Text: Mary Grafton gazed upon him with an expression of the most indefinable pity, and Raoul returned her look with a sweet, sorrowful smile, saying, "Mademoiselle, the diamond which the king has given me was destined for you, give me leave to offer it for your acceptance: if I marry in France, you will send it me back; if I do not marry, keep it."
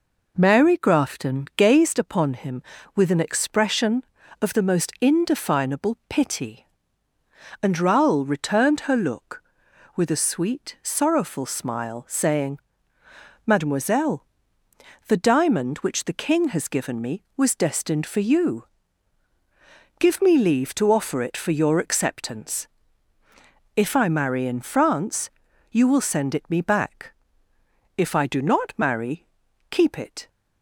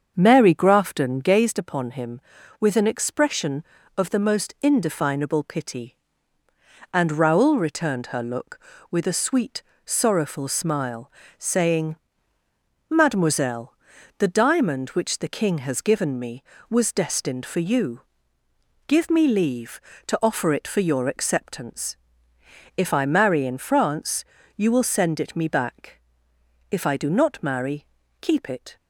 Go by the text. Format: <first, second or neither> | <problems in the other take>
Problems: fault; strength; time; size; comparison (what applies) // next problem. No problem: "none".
first | starts louder than the rest; until 1.5 s; 7 dB